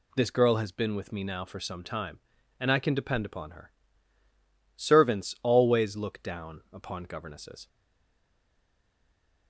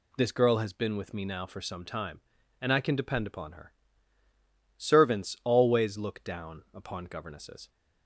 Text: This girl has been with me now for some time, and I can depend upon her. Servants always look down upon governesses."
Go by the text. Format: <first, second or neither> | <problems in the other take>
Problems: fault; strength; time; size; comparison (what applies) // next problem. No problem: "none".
second | stays silent after the last word; noticeable; from 7.6 s on; 1.8 s long